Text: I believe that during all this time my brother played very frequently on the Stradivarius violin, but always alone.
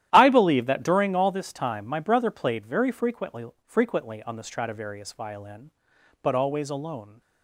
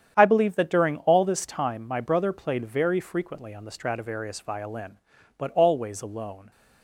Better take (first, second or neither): second